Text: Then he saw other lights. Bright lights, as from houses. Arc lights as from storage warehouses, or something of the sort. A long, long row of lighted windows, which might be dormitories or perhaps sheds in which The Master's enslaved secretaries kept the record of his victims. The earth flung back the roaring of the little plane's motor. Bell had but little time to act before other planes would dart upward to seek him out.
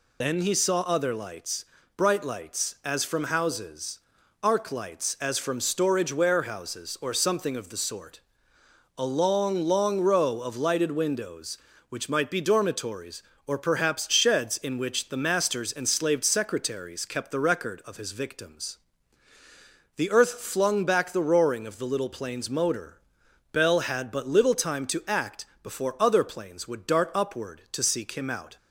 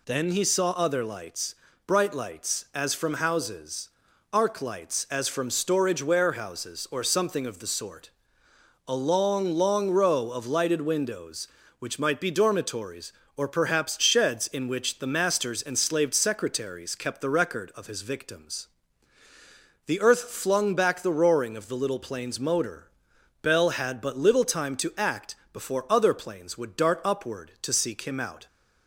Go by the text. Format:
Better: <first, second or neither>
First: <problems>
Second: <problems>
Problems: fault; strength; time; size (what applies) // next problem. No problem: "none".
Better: second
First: loses the start of "Then"; at 0.2 s; 40 ms // pauses between "act" and "before"; slight; at 25.4 s; 0.18 s long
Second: pauses between "act" and "before"; slight; at 25.3 s; 0.18 s long